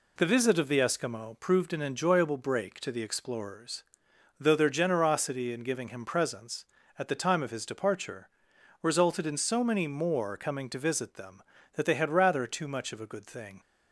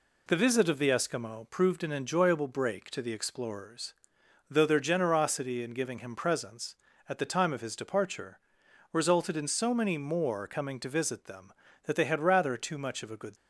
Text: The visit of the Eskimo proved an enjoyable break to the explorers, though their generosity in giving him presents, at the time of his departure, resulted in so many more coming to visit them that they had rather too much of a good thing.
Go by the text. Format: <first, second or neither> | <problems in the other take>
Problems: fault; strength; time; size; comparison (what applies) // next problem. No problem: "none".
first | stops before "thing"; at 13.3 s